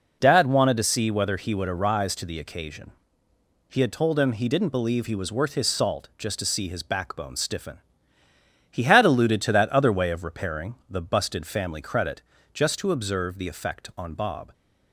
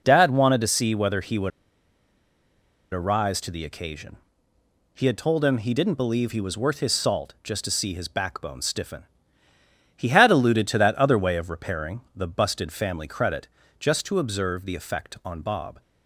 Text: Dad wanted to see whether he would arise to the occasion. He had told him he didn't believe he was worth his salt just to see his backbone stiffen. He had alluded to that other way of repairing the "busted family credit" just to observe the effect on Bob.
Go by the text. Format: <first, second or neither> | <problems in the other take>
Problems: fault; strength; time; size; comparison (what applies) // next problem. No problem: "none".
first | pauses between "would" and "arise"; strong; at 1.5 s; 1.4 s long // pauses between "repairing" and "the"; slight; at 11.9 s; 0.16 s long; slight in the first // pauses between "credit" and "just"; slight; at 13.4 s; 0.30 s long; slight in the first